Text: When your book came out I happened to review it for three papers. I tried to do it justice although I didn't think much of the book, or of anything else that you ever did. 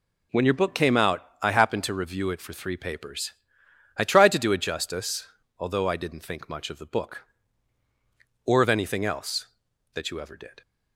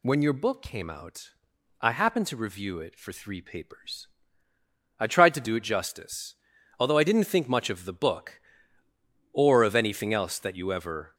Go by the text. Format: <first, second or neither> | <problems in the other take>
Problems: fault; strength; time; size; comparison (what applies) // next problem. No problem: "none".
first | pauses between "out" and "I"; noticeable; at 1.3 s; 0.50 s long; slight in the first // pauses between "justice" and "although"; at 6.3 s; 0.42 s long; slight in the first // stops before "did"; at 11.1 s